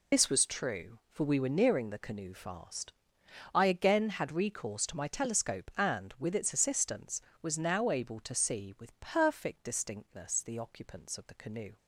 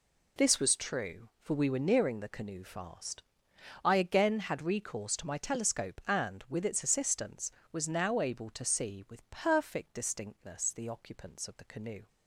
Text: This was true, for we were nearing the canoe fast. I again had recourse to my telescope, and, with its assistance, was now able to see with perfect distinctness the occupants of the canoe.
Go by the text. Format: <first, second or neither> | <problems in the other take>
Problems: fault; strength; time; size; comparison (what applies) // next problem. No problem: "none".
second | loses the start of "This"; at 0.1 s; 65 ms